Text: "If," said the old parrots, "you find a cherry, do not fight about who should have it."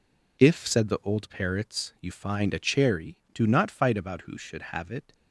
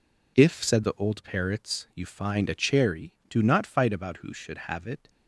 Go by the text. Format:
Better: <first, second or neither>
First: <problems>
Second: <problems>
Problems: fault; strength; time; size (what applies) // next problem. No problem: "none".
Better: neither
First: none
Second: none